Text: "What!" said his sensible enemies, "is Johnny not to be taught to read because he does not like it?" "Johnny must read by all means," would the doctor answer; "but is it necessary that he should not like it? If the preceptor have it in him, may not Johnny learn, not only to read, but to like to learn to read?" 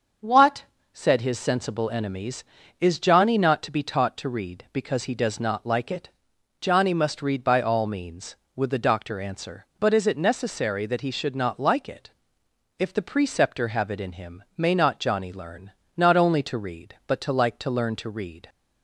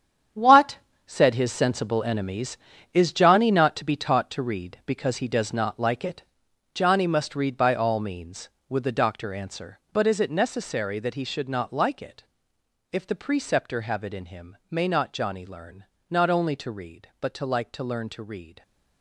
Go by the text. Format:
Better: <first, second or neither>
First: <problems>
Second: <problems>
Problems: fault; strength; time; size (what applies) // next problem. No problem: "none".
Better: first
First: starts louder than the rest; until 1.4 s; 6.5 dB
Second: gets quieter; strong; throughout; 11.5 dB // starts louder than the rest; strong; until 1.6 s; 9 dB